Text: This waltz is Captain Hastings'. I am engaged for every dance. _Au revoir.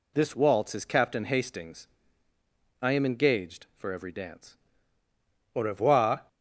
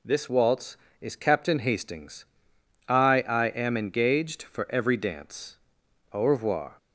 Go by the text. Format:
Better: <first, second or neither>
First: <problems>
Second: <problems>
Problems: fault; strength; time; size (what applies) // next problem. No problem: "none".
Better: first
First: none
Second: says "I" twice; at 3.2 s